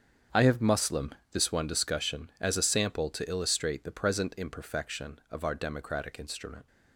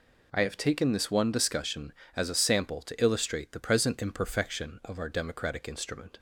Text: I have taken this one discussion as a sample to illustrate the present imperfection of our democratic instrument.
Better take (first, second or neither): second